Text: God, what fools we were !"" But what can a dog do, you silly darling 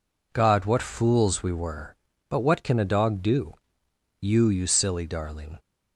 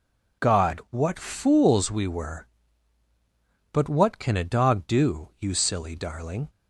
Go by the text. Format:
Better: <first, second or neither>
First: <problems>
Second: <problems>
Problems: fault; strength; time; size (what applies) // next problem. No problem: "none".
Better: second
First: says "you" twice; at 4.4 s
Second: none